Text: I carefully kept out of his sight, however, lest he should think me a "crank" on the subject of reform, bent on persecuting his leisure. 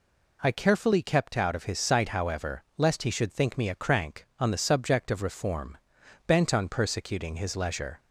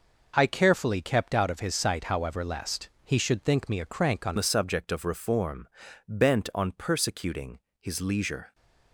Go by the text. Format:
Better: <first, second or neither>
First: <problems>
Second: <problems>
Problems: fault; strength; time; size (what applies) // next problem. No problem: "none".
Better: first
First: none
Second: pauses between "lest" and "he"; slight; at 2.8 s; 0.16 s long // changes voice at "the"; from 4.3 s on; 4.2 s long // pauses between "persecuting" and "his"; slight; at 7.5 s; 0.22 s long